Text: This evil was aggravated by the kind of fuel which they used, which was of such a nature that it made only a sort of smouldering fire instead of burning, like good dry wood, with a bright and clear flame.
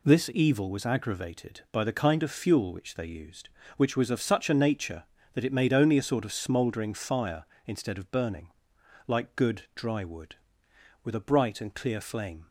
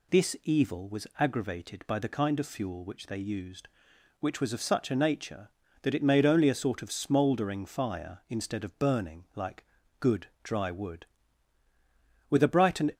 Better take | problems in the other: first | pauses between "like" and "good"; slight; at 9.6 s; 0.36 s long // pauses between "good" and "dry"; slight; at 10.2 s; 0.18 s long // stops before "clear flame"; at 12.9 s

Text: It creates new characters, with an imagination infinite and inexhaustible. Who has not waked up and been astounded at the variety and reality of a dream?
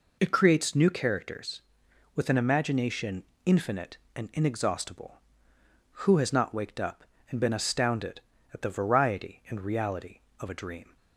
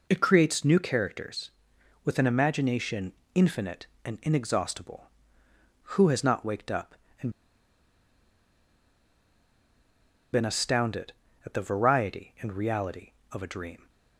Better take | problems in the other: first | pauses between "imagination" and "infinite"; slight; at 3.1 s; 0.22 s long; slight in the first // pauses between "and" and "been"; strong; at 7.2 s; 3.0 s long

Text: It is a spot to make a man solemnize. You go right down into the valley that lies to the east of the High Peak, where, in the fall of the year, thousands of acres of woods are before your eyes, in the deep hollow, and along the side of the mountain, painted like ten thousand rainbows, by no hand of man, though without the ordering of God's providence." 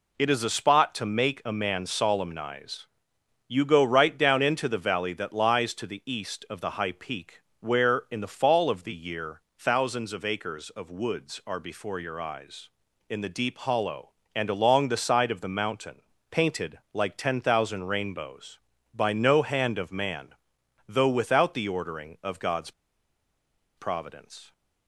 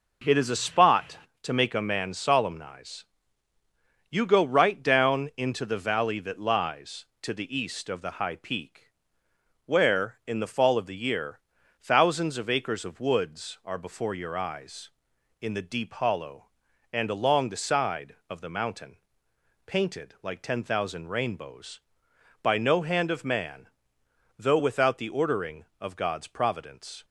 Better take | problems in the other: second | pauses between "God's" and "providence"; at 22.7 s; 1.0 s long

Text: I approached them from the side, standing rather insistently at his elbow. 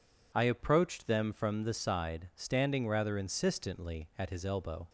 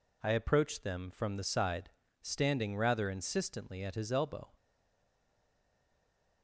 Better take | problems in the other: first | stays silent after the last word; noticeable; from 4.5 s on; 1.9 s long

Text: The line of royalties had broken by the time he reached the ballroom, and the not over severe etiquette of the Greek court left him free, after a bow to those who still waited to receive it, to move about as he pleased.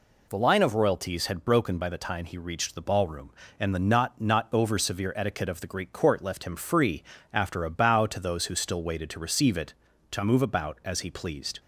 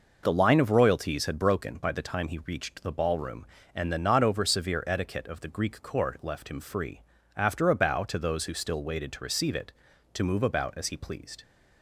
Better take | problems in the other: second | says "not" twice; at 4.1 s

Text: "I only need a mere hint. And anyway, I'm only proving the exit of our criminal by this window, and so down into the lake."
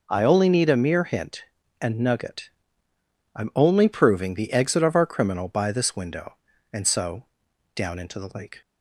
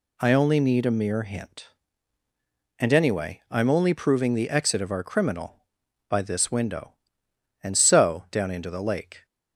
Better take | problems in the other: second | says "nugget" for "anyway"; at 1.9 s // pauses between "so" and "down"; noticeable; at 7.2 s; 0.50 s long

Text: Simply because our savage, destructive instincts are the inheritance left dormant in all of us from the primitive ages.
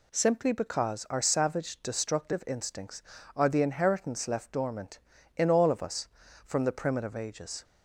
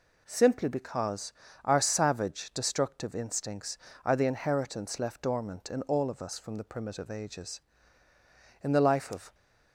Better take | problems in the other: first | pauses between "because" and "our"; slight; at 1.3 s; 0.32 s long // goes on to say "In the life of"; noticeable; from 8.6 s on; 0.72 s long

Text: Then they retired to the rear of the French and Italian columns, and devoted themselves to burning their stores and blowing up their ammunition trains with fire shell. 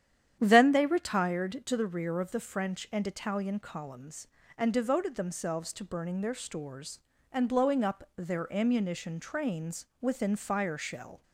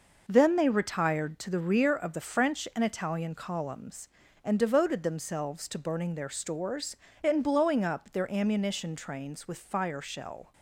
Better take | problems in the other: second | starts louder than the rest; strong; until 1.4 s; 10 dB // says "within" for "with"; at 10.0 s

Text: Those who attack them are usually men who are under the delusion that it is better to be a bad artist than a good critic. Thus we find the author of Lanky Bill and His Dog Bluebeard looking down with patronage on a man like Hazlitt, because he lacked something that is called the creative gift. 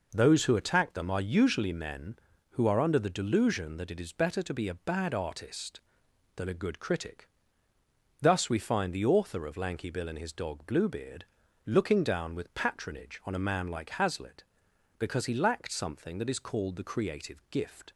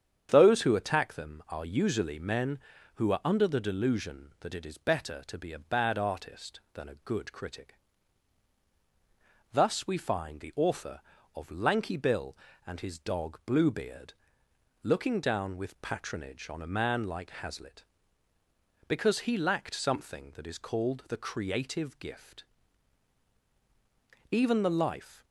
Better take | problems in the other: first | starts louder than the rest; strong; until 1.3 s; 8 dB // pauses between "Bluebeard" and "looking"; noticeable; at 14.1 s; 0.70 s long; also in the first // goes on to say "Even the life"; noticeable; from 24.2 s on; 0.94 s long

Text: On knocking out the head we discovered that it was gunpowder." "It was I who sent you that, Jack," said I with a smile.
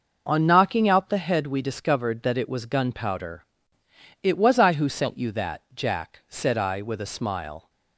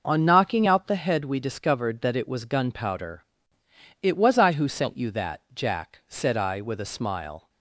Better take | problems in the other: neither | none

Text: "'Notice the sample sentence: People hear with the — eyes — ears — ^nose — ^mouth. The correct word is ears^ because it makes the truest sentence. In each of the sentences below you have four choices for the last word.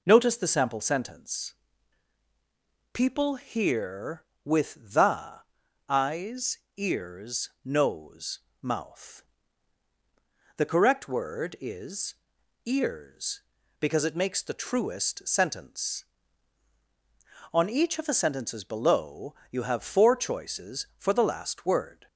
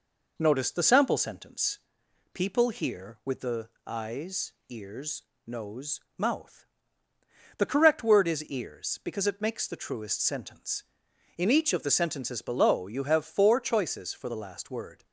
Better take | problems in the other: second | pauses between "is" and "ears"; noticeable; at 12.1 s; 0.50 s long // says "On" for "In"; at 17.5 s // pauses between "below" and "you"; slight; at 19.3 s; 0.16 s long

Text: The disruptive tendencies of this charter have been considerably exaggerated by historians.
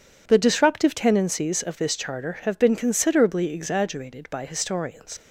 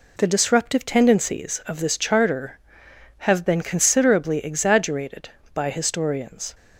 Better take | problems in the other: second | leaves "historians" unfinished; at 5.1 s; 85 ms

